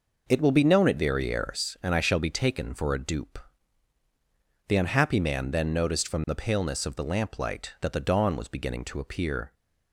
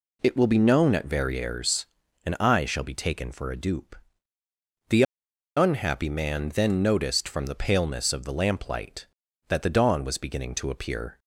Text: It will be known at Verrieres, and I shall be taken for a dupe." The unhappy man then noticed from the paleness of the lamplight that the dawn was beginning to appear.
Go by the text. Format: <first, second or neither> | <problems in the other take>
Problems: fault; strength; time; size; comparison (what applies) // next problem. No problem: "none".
first | pauses between "The" and "unhappy"; noticeable; at 5.0 s; 0.53 s long